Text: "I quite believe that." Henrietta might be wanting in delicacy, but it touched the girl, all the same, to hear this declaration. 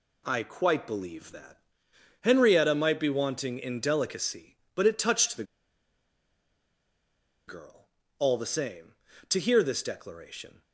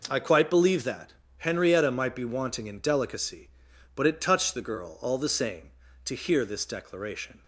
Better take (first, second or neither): second